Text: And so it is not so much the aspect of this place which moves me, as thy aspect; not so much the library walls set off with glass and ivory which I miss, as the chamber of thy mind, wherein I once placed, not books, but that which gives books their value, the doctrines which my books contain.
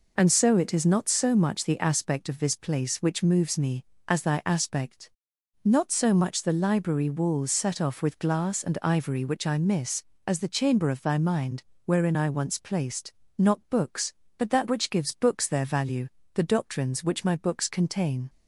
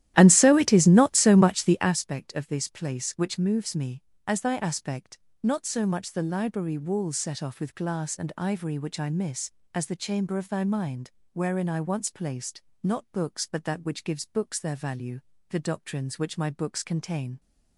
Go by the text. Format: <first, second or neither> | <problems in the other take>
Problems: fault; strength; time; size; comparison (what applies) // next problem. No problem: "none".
first | starts louder than the rest; strong; until 2.0 s; 13 dB